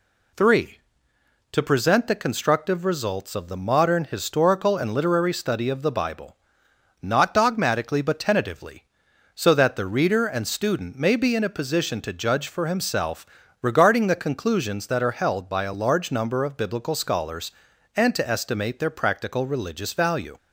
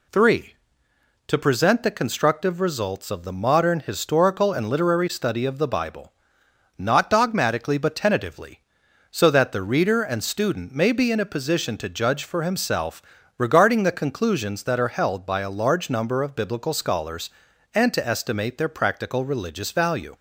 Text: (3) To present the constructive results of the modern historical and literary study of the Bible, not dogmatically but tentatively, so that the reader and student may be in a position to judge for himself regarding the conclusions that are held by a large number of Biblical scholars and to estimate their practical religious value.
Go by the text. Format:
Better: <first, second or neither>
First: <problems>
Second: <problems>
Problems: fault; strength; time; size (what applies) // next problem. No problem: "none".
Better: neither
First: pauses between "himself" and "regarding"; slight; at 13.2 s; 0.34 s long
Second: pauses between "himself" and "regarding"; slight; at 13.0 s; 0.34 s long